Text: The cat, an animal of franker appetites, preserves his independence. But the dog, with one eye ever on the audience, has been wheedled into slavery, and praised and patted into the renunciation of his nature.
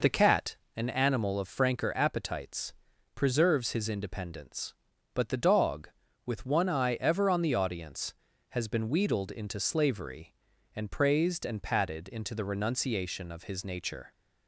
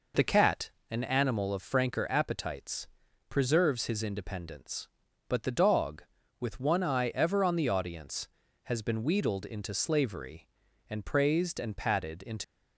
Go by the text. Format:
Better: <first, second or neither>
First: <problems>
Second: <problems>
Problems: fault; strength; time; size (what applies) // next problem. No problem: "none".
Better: first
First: none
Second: stops before "the renunciation of his nature"; at 12.4 s